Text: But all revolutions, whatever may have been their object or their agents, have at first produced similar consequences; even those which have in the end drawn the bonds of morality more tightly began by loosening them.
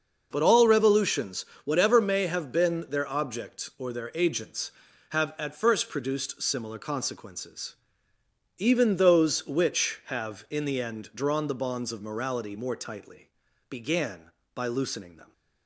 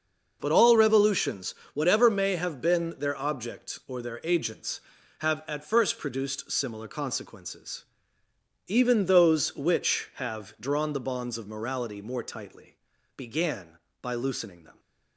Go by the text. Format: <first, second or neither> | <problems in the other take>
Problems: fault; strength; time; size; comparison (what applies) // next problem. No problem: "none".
first | starts louder than the rest; noticeable; until 1.4 s; 6 dB; noticeable in the first // skips "in the end"; at 10.5 s // pauses between "tightly" and "began"; at 12.7 s; 0.40 s long; also in the first